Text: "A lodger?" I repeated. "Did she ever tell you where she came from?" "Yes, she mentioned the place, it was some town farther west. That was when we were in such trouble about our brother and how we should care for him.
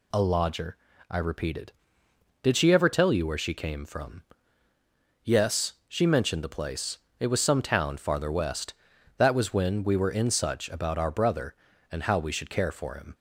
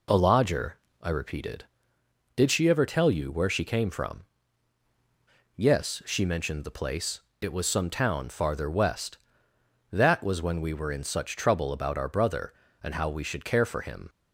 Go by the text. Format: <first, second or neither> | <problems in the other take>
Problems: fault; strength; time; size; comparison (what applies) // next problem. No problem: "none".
second | skips "trouble"; at 10.6 s